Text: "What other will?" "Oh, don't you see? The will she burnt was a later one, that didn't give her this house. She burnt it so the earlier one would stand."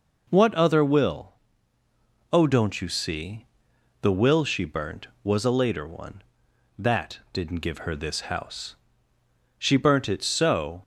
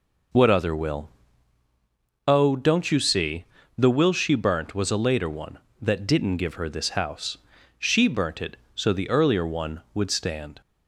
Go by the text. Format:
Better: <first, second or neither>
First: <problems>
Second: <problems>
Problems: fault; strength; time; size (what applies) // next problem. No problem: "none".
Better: second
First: stops before "the earlier one would stand"; at 10.8 s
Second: none